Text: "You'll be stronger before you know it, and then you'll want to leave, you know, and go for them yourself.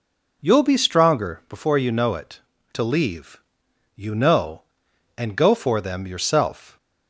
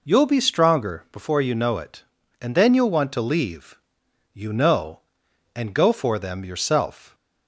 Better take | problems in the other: second | skips "and then you'll want"; at 2.5 s

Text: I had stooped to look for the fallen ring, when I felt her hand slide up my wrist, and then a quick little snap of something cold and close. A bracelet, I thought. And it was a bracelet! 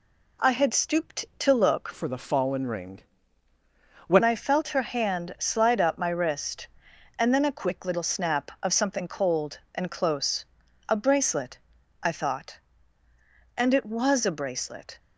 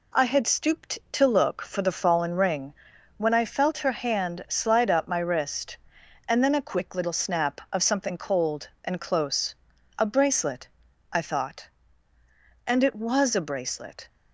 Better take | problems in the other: second | changes voice from "for" to "when"; from 1.9 to 4.2 s; 2.3 s long

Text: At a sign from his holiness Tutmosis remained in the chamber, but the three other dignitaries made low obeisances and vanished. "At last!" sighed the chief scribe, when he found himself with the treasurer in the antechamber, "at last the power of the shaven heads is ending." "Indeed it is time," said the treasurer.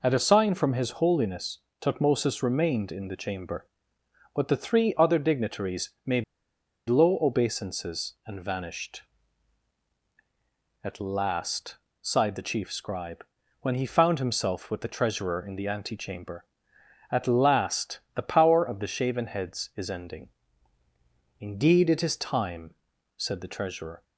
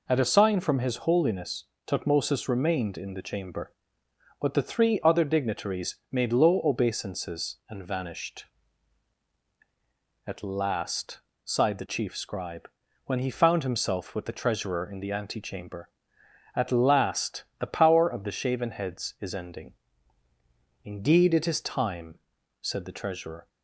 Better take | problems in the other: second | pauses between "holiness" and "Tutmosis"; slight; at 1.5 s; 0.22 s long; slight in the second // pauses between "dignitaries" and "made"; slight; at 5.9 s; 0.16 s long; slight in the second // pauses between "made" and "low"; noticeable; at 6.2 s; 0.65 s long // pauses between "last" and "the"; slight; at 17.9 s; 0.16 s long; slight in the second

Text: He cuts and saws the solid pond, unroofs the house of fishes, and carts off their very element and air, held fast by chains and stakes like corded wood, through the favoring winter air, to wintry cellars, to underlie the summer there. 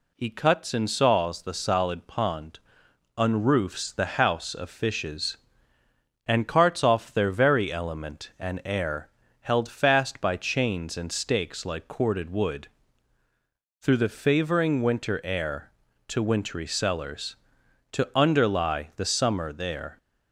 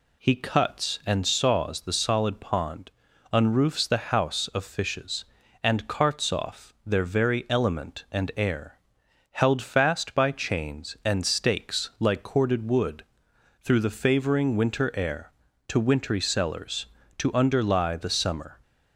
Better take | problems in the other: first | stops before "there"; at 18.6 s

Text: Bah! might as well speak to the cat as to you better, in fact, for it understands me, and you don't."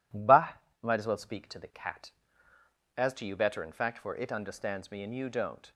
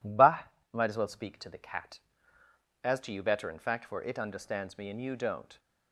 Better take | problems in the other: neither | none

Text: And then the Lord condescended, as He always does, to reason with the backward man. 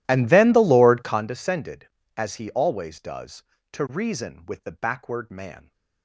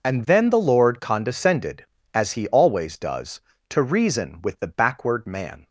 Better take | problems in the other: second | starts louder than the rest; strong; until 1.4 s; 14 dB

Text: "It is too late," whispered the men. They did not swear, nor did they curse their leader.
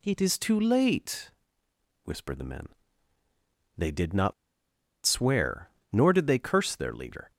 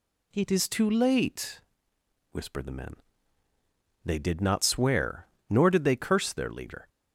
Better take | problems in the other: second | pauses between "not" and "swear"; noticeable; at 4.3 s; 0.73 s long

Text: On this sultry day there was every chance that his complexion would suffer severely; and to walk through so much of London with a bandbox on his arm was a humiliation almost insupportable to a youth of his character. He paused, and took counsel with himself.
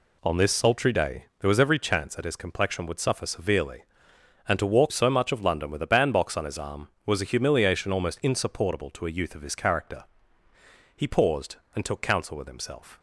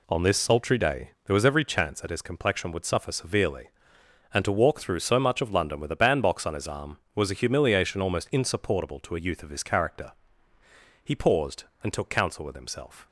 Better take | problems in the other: second | skips "through"; at 4.9 s

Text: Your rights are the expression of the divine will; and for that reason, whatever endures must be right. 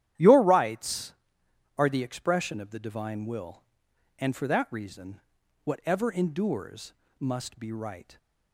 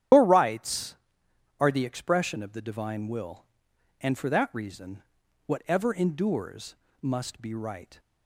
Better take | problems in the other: first | loses the start of "Your"; at 0.1 s; 125 ms // starts louder than the rest; strong; until 1.7 s; 10.5 dB; strong in the first // pauses between "endures" and "must"; slight; at 6.7 s; 0.26 s long; slight in the first

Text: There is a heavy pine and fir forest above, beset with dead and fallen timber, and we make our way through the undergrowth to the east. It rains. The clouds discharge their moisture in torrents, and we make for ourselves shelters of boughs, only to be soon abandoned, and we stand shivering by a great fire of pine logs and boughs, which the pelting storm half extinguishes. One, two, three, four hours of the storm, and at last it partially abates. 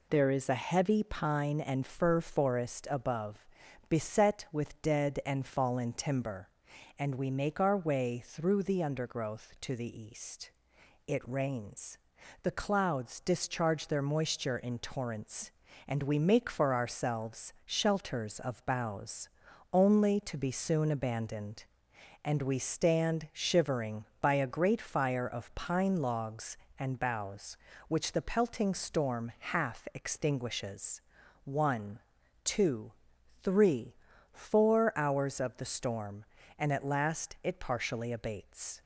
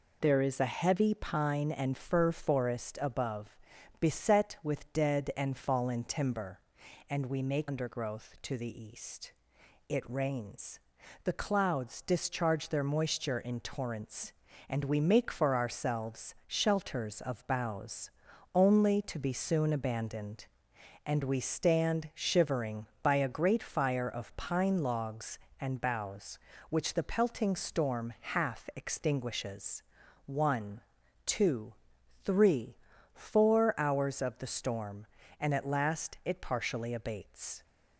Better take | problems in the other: first | skips "our way through the"; at 7.6 s

